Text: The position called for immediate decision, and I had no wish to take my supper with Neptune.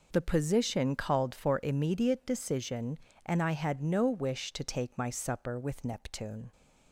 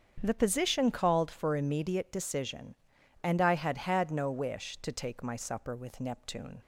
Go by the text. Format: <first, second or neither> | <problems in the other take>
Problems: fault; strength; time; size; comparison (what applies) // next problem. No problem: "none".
first | starts louder than the rest; strong; until 1.2 s; 7.5 dB // says "had" twice; at 3.7 s